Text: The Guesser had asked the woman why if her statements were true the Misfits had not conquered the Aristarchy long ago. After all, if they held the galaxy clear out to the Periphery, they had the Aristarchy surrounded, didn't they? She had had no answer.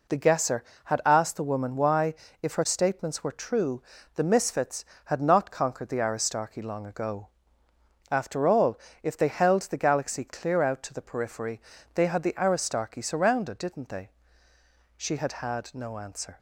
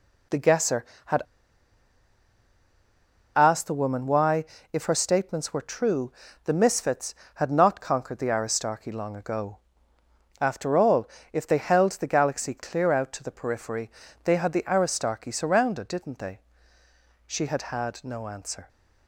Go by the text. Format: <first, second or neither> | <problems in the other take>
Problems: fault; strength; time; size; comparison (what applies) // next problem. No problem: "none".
first | pauses between "had" and "asked"; strong; at 1.2 s; 2.1 s long // pauses between "why" and "if"; slight; at 4.4 s; 0.28 s long; slight in the first // pauses between "true" and "the"; slight; at 6.1 s; 0.32 s long; slight in the first